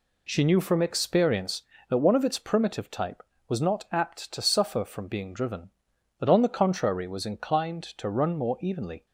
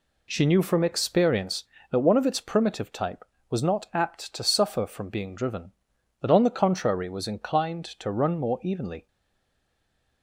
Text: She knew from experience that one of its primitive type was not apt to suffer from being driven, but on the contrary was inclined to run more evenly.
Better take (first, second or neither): first